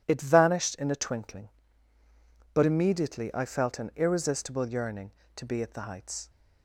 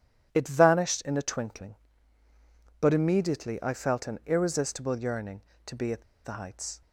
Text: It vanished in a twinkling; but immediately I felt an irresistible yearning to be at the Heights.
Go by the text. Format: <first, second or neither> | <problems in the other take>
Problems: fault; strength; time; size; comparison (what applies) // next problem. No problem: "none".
first | pauses between "at" and "the"; slight; at 6.0 s; 0.21 s long